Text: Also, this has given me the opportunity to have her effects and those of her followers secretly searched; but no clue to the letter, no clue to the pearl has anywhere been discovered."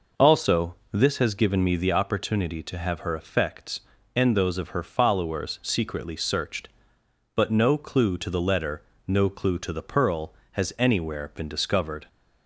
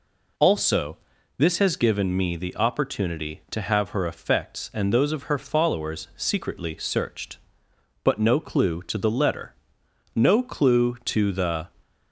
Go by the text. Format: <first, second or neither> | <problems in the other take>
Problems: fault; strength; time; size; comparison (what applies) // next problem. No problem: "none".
first | stops before "pearl has anywhere been discovered"; at 11.8 s